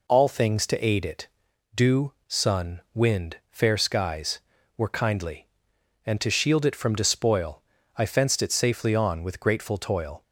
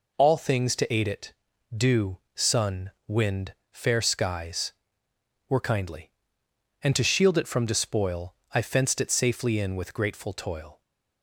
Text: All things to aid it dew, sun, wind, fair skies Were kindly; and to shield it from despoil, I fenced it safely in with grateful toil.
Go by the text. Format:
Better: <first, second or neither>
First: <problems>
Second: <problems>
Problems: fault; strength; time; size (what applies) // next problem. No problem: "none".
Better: second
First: pauses between "it" and "dew"; noticeable; at 1.2 s; 0.48 s long // says "on" for "in"; at 8.9 s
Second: pauses between "it" and "dew"; at 1.3 s; 0.42 s long